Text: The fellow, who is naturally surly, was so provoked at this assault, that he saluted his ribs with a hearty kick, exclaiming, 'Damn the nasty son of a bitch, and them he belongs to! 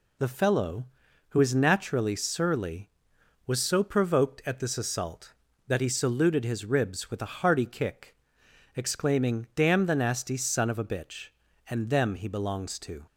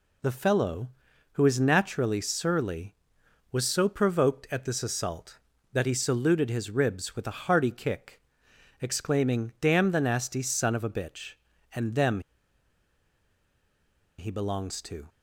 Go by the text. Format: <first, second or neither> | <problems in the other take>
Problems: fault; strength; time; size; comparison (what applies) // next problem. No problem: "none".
first | pauses between "them" and "he"; strong; at 12.1 s; 1.9 s long